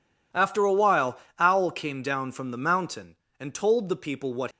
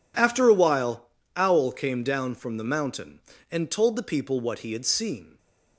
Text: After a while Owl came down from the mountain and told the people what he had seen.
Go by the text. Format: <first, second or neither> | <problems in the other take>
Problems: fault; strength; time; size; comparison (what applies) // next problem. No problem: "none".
second | pauses between "while" and "Owl"; slight; at 1.1 s; 0.22 s long; slight in the second // stops before "he had seen"; at 4.5 s